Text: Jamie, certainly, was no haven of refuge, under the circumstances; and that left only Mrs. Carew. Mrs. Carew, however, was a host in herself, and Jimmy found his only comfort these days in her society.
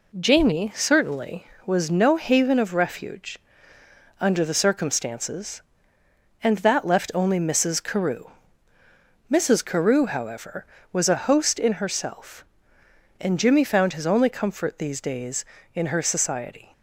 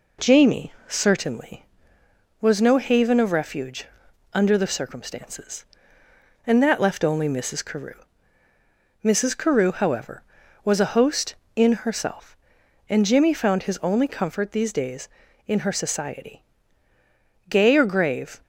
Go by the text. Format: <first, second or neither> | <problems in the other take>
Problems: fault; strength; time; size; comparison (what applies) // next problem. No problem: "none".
first | goes on to say "Gay or grave"; noticeable; from 17.4 s on; 0.94 s long